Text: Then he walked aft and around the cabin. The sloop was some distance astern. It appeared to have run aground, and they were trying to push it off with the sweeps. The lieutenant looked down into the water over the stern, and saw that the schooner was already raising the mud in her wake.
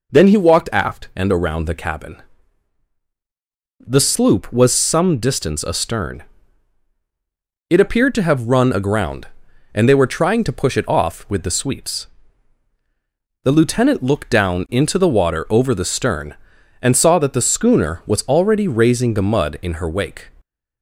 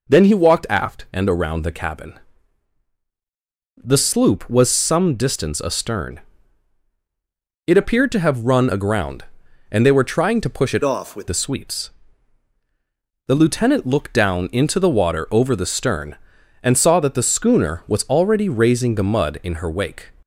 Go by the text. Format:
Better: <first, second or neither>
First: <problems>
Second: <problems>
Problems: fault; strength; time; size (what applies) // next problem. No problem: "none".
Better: first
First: none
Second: changes voice from "off" to "with"; from 10.8 to 11.2 s; 0.4 s long